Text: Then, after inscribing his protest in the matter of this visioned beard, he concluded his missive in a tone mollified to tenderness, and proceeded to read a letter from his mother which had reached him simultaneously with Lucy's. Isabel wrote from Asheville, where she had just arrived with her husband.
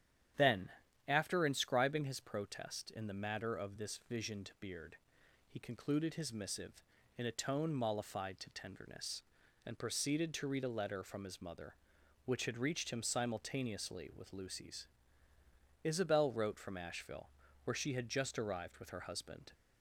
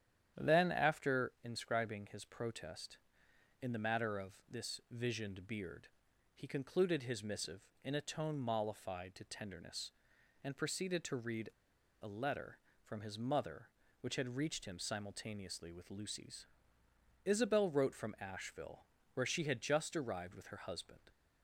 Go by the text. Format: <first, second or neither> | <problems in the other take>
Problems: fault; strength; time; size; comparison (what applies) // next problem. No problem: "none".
first | starts louder than the rest; strong; until 1.4 s; 10 dB; strong in the first // pauses between "read" and "a"; noticeable; at 11.5 s; 0.51 s long